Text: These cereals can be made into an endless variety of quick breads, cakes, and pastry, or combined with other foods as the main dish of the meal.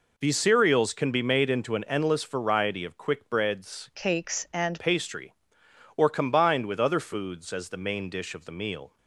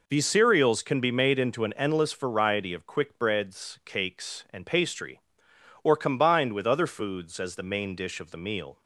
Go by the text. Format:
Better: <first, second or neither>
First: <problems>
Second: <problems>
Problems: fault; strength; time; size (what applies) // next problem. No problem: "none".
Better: second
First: changes voice from "cakes" to "and"; from 3.9 to 4.8 s; 0.9 s long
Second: none